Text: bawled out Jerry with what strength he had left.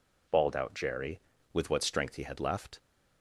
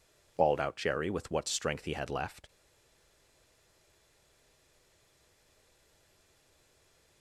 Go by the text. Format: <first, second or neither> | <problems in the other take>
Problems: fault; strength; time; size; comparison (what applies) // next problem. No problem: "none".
first | stays silent after the last word; strong; from 2.4 s on; 4.8 s long